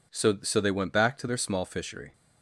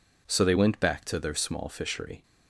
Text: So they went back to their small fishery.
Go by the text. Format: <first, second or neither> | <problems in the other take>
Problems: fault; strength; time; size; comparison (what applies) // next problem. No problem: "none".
second | says "So" twice; at 0.4 s